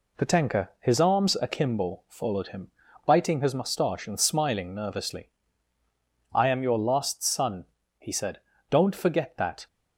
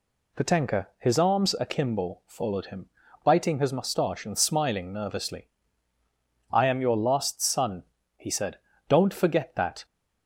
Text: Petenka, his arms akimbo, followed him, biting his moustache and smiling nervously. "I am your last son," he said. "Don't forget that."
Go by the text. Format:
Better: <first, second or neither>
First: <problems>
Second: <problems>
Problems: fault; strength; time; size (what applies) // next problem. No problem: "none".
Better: second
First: gets quieter; throughout; 3.5 dB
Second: none